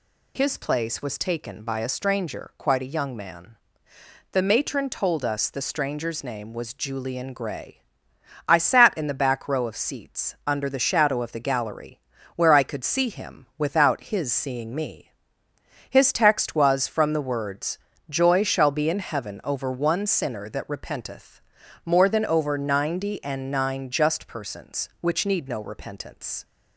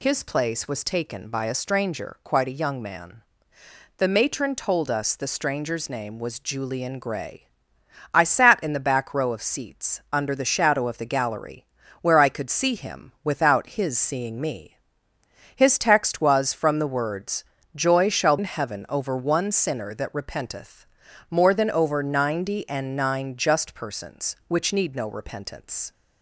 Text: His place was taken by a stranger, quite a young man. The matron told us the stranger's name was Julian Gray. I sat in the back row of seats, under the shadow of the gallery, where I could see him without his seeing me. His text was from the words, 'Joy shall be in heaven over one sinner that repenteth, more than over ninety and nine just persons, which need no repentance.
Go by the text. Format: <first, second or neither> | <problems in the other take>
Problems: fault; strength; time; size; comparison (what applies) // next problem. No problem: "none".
first | skips "be"; at 18.3 s